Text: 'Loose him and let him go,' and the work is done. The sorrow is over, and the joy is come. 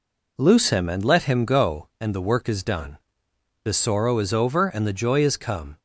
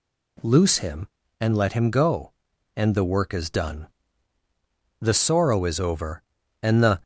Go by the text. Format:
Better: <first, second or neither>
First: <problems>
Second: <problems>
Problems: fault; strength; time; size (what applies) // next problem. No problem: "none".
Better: first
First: none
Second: stops before "joy is come"; at 7.0 s